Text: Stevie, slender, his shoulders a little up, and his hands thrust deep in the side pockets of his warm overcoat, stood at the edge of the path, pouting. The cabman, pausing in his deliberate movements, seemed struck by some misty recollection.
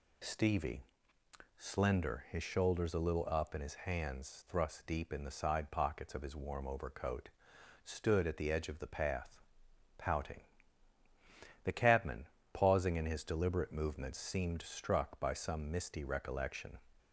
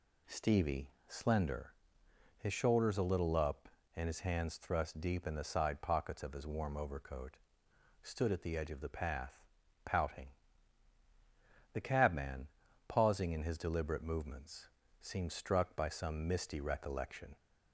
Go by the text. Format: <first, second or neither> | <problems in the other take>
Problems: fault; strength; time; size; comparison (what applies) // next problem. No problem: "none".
neither | none